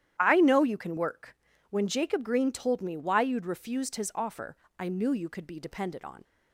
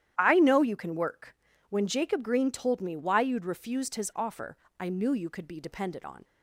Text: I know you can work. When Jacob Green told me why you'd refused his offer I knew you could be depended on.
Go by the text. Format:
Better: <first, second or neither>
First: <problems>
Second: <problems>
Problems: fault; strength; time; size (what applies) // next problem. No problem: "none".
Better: neither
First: starts louder than the rest; strong; until 1.2 s; 11.5 dB // pauses between "offer" and "I"; slight; at 4.5 s; 0.22 s long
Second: starts louder than the rest; strong; until 1.1 s; 11.5 dB // pauses between "offer" and "I"; slight; at 4.5 s; 0.22 s long